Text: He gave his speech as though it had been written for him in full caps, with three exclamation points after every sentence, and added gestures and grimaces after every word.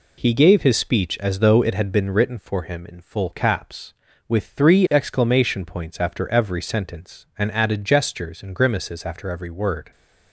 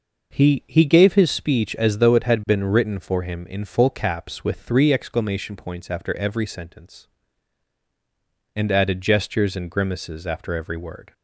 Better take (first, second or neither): first